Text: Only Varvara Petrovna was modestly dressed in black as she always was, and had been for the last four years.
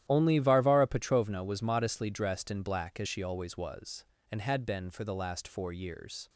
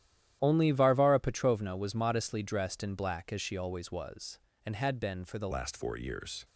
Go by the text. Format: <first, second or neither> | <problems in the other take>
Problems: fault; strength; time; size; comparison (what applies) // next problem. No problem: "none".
first | starts louder than the rest; strong; until 1.4 s; 11.5 dB; strong in the first // changes voice at "last"; from 5.5 s on; 0.9 s long